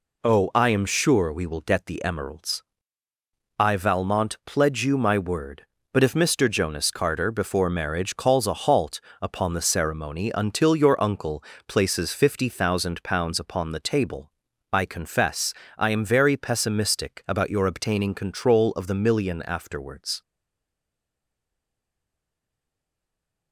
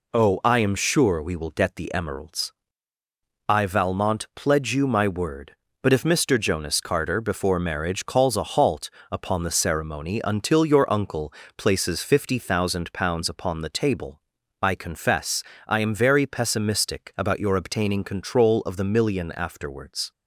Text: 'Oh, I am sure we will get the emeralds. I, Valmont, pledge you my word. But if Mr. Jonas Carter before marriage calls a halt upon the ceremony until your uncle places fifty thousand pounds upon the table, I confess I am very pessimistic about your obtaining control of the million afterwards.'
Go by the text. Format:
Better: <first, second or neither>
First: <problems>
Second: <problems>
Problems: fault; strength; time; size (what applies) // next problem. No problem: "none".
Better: second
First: pauses between "halt" and "upon"; slight; at 8.9 s; 0.22 s long // pauses between "uncle" and "places"; slight; at 11.4 s; 0.26 s long // pauses between "confess" and "I"; slight; at 15.5 s; 0.24 s long // stays silent after the last word; strong; from 20.2 s on; 3.3 s long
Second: pauses between "halt" and "upon"; slight; at 8.8 s; 0.22 s long // pauses between "uncle" and "places"; slight; at 11.3 s; 0.26 s long // pauses between "confess" and "I"; slight; at 15.4 s; 0.24 s long